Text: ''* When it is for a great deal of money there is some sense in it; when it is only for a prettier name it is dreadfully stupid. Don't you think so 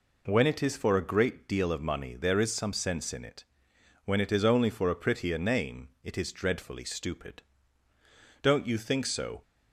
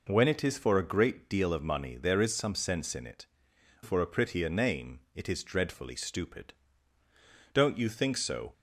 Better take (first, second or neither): first